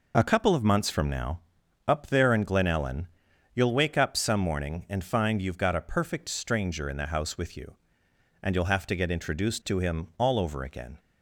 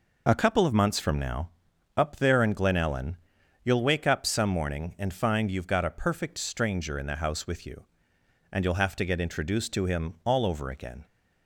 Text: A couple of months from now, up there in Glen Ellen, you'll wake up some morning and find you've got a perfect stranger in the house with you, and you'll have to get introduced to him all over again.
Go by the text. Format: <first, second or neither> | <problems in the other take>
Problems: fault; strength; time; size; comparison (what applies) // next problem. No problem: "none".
neither | none